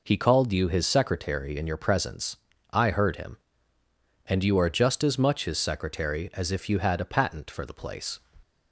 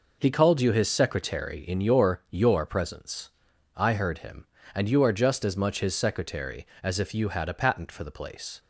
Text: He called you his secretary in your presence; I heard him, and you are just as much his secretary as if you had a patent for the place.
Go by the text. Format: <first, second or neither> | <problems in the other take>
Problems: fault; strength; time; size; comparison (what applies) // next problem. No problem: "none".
first | says "your" twice; at 2.2 s